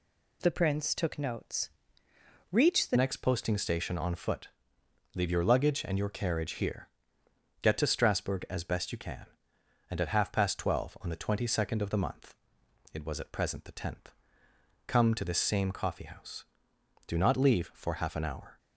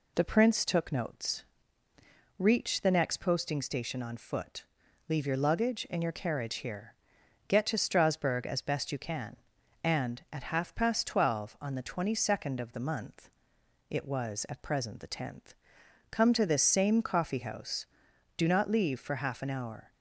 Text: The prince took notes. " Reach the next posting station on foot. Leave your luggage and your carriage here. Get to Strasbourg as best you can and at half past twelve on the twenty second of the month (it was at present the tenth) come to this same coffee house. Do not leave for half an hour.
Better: second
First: changes voice at "next"; from 2.9 s on; 15.6 s long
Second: none

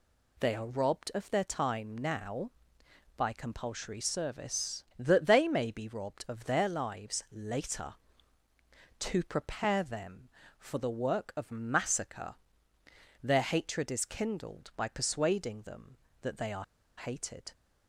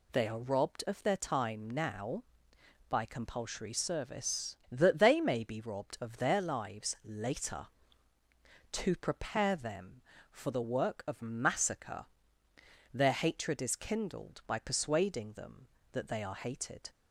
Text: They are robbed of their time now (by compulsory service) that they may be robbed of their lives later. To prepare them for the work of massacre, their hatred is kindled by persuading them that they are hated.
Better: second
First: pauses between "are" and "hated"; slight; at 16.6 s; 0.33 s long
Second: none

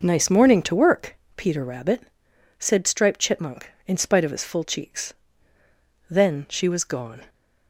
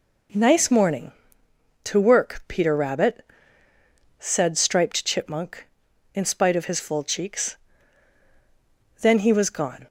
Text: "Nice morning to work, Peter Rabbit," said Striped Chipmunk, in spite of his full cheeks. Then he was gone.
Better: second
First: says "she" for "he"; at 6.4 s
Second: none

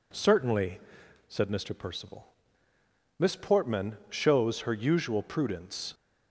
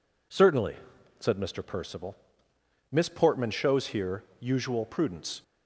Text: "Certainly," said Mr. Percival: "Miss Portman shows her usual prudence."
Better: first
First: none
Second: says "here" for "her"; at 3.8 s

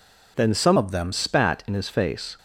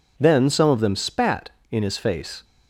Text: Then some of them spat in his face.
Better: second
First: changes voice from "of" to "them"; from 0.7 to 1.1 s; 0.4 s long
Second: none

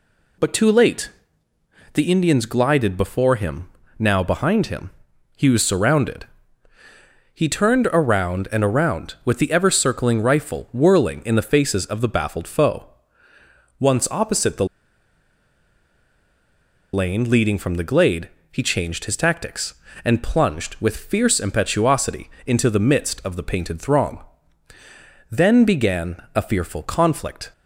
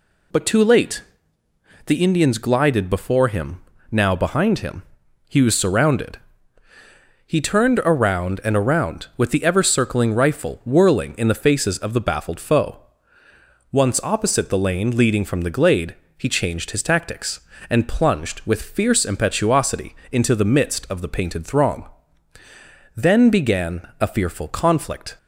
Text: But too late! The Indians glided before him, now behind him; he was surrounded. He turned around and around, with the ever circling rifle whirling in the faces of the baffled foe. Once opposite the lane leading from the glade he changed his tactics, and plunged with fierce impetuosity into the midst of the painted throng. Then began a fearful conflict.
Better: second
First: pauses between "the" and "lane"; strong; at 14.6 s; 2.2 s long // pauses between "glade" and "he"; slight; at 18.2 s; 0.22 s long // pauses between "impetuosity" and "into"; slight; at 22.2 s; 0.18 s long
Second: pauses between "glade" and "he"; slight; at 15.9 s; 0.22 s long // pauses between "impetuosity" and "into"; slight; at 19.9 s; 0.18 s long

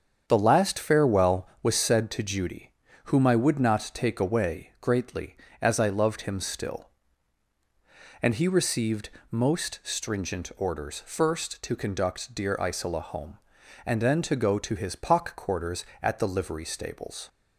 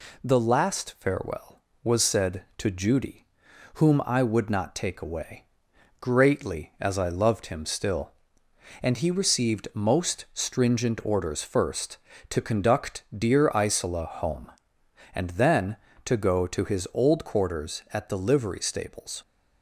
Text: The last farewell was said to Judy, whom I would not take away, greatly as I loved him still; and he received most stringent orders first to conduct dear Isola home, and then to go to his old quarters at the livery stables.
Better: second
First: starts louder than the rest; strong; until 1.2 s; 7.5 dB // pauses between "received" and "most"; slight; at 9.0 s; 0.20 s long // says "pock" for "old"; at 14.9 s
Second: none

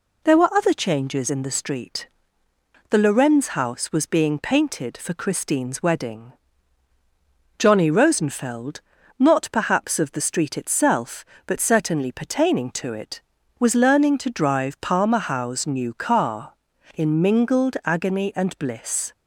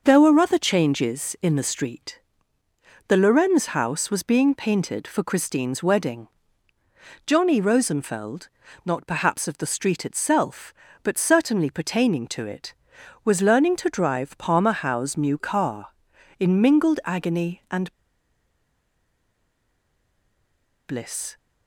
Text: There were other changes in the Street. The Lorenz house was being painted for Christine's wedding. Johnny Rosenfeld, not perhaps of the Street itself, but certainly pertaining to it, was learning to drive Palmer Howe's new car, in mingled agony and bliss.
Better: first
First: none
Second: pauses between "and" and "bliss"; strong; at 17.9 s; 2.9 s long

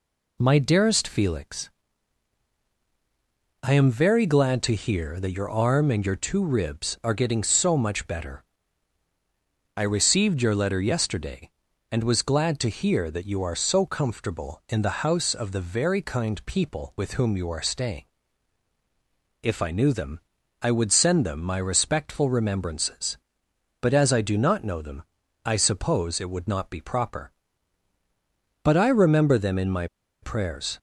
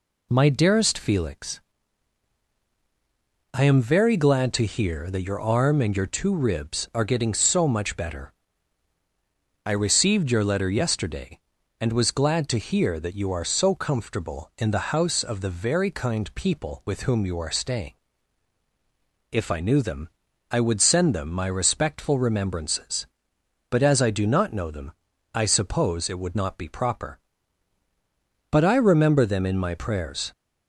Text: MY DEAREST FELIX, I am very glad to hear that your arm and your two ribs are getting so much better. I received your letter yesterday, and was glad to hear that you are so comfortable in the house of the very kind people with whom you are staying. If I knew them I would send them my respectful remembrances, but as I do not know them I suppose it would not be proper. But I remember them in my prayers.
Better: second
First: pauses between "them" and "I"; at 20.1 s; 0.42 s long // pauses between "them" and "I"; at 25.0 s; 0.42 s long // pauses between "my" and "prayers"; at 29.8 s; 0.36 s long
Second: pauses between "them" and "I"; at 20.0 s; 0.42 s long // pauses between "them" and "I"; at 24.9 s; 0.42 s long

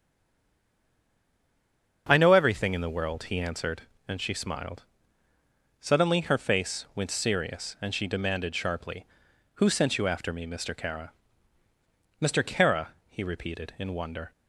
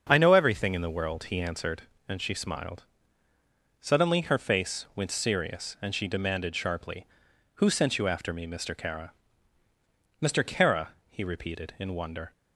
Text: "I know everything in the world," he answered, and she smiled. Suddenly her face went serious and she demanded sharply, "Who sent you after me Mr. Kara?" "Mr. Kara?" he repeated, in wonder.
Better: second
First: stays silent before the first word; noticeable; until 2.0 s; 2.0 s long // starts louder than the rest; until 3.1 s; 7 dB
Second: starts louder than the rest; until 1.1 s; 7 dB

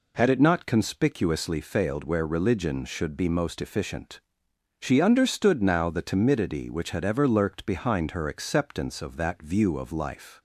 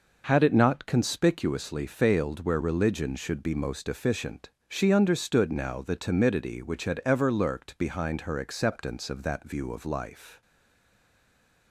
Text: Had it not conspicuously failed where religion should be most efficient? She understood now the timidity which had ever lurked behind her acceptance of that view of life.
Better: first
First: none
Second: stays silent after the last word; noticeable; from 10.4 s on; 1.3 s long

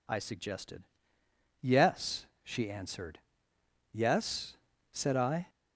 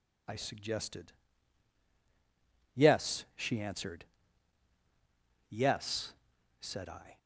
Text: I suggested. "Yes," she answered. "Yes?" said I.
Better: neither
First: none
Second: none

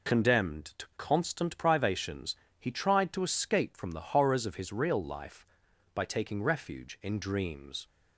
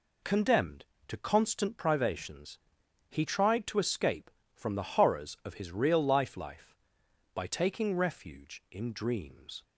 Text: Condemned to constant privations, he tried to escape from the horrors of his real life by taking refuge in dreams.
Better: first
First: none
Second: says "life" twice; at 6.3 s

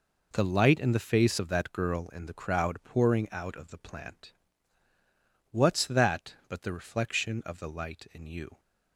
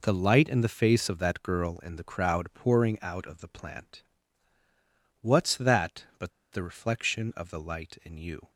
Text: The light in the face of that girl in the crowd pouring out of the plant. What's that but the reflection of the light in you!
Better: first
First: none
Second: pauses between "but" and "the"; slight; at 6.3 s; 0.21 s long

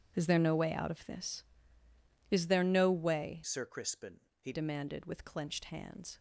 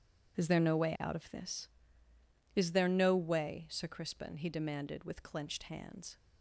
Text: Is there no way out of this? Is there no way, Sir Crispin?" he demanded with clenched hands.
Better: second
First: changes voice from "Sir" to "he"; from 3.4 to 4.5 s; 1.1 s long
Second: none

